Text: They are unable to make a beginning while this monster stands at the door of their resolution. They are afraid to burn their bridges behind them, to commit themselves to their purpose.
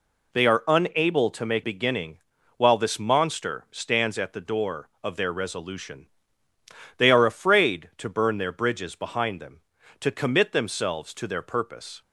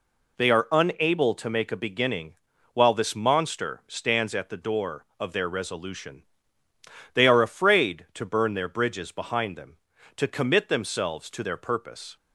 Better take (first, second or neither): second